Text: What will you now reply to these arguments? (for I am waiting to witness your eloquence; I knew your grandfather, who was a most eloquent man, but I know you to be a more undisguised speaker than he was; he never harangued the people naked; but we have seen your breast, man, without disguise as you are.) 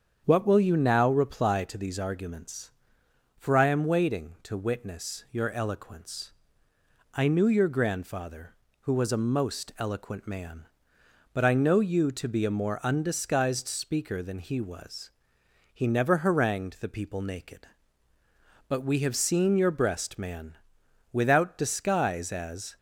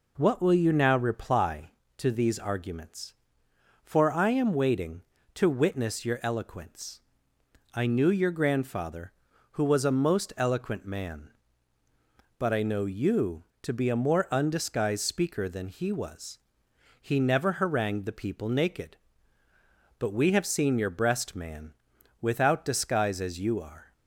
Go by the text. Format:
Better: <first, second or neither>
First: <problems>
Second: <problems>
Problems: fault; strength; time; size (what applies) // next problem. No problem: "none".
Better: second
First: starts louder than the rest; strong; until 1.2 s; 7.5 dB // stops before "you are"; at 22.7 s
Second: none